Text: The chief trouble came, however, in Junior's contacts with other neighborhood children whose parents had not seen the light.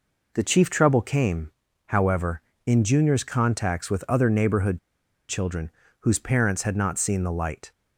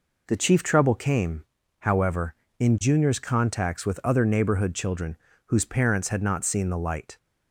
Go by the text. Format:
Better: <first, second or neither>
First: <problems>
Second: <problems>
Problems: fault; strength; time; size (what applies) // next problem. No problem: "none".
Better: second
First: pauses between "neighborhood" and "children"; noticeable; at 4.7 s; 0.49 s long // pauses between "children" and "whose"; slight; at 5.6 s; 0.30 s long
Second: pauses between "children" and "whose"; slight; at 5.1 s; 0.30 s long